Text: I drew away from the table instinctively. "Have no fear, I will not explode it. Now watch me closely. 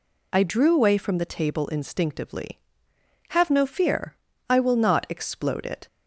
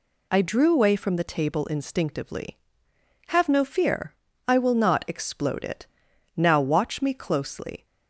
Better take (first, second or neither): second